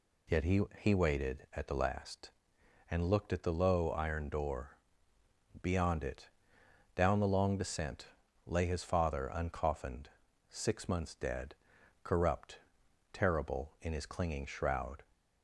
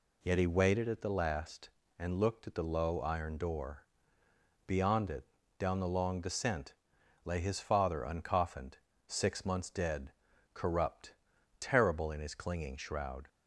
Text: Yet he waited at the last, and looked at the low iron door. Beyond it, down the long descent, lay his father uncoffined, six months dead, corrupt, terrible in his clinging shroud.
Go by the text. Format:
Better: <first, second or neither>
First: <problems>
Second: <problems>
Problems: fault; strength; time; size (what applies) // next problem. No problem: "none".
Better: second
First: says "he" twice; at 0.7 s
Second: none